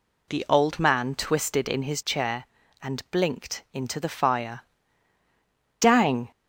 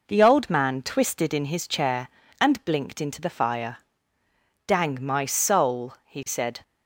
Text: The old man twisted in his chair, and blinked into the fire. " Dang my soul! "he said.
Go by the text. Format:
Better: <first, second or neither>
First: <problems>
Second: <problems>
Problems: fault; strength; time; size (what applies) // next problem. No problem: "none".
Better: second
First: stops before "my soul he said"; at 6.3 s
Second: none